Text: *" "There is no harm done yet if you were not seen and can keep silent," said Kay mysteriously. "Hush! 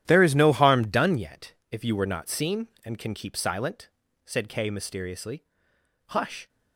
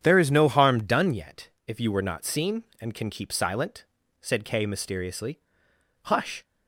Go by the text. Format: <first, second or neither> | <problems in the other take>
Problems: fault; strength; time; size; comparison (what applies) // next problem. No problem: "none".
second | gets quieter; strong; throughout; 13 dB // starts louder than the rest; strong; until 1.0 s; 11 dB; strong in the second // pauses between "yet" and "if"; slight; at 1.5 s; 0.18 s long; slight in the second